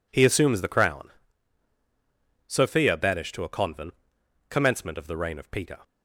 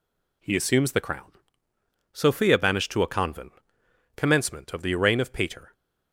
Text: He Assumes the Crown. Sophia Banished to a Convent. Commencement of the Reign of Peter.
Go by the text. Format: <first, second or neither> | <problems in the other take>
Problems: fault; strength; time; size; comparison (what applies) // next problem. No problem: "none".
neither | none